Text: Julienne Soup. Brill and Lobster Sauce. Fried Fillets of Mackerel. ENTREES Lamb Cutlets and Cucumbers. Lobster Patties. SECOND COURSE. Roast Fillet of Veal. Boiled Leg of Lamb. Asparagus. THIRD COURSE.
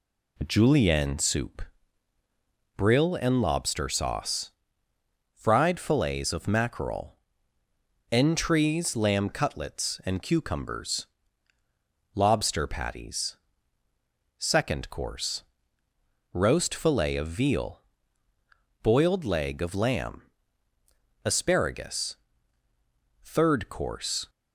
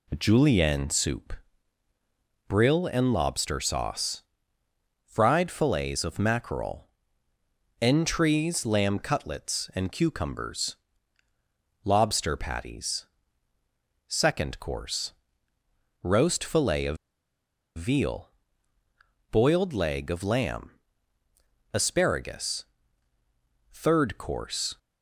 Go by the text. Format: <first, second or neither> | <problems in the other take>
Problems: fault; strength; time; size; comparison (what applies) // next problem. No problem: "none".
first | pauses between "of" and "Veal"; noticeable; at 16.9 s; 0.79 s long